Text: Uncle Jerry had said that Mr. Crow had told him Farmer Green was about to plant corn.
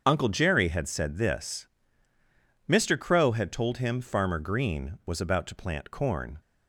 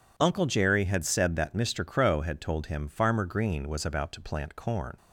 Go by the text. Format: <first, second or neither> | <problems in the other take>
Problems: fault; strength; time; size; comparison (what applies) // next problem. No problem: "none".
second | starts louder than the rest; until 1.0 s; 6.5 dB // says "this" for "that"; at 1.1 s